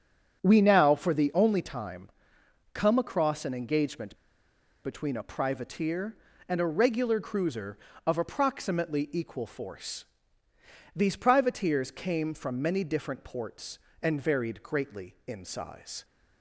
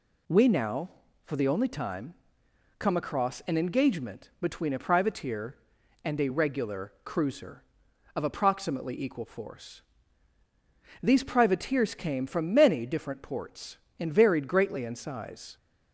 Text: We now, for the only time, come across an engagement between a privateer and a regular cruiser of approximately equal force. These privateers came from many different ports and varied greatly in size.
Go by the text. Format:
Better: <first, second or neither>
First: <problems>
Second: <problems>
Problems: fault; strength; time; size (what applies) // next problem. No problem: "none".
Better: second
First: starts louder than the rest; strong; until 1.4 s; 7.5 dB // pauses between "engagement" and "between"; noticeable; at 4.1 s; 0.68 s long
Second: none